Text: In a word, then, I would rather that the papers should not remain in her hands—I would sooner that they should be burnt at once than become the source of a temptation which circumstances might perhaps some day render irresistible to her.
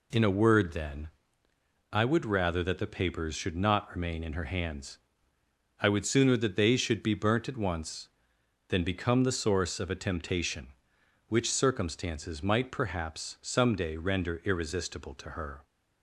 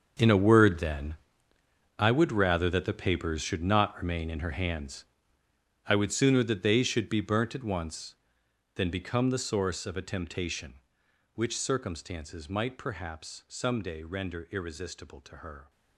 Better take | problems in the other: first | gets quieter; strong; throughout; 14.5 dB

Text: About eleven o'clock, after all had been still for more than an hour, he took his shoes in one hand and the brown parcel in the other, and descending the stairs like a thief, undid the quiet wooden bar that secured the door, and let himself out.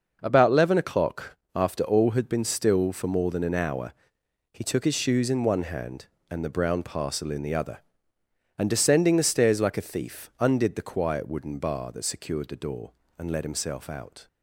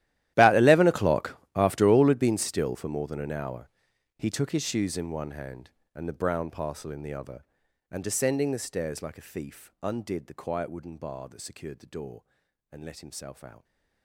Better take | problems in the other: first | gets quieter; strong; throughout; 20.5 dB

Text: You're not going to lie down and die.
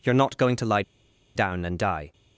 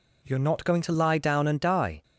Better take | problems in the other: second | pauses between "lie" and "down"; noticeable; at 0.8 s; 0.53 s long

